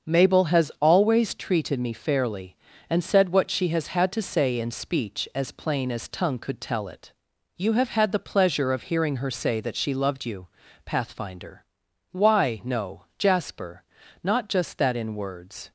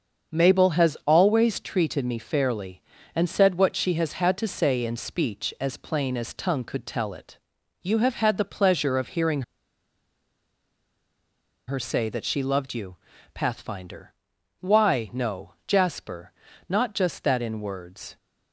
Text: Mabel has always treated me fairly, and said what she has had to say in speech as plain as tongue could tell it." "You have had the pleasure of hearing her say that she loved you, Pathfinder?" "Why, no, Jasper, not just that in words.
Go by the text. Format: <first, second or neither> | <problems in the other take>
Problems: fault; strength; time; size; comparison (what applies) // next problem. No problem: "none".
first | starts louder than the rest; until 1.4 s; 7 dB; also in the first // pauses between "hearing" and "her"; strong; at 9.4 s; 2.2 s long